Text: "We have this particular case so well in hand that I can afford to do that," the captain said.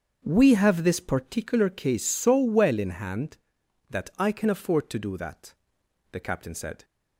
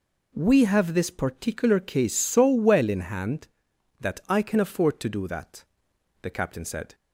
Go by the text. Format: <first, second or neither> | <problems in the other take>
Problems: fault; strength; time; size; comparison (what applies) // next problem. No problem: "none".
second | starts louder than the rest; until 1.4 s; 7 dB